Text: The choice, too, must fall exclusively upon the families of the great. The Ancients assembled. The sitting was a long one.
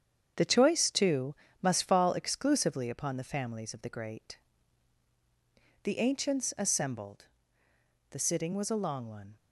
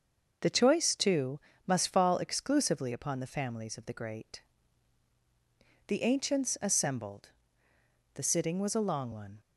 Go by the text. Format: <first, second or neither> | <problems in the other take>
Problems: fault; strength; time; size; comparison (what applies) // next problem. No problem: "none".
second | gets quieter; strong; throughout; 7 dB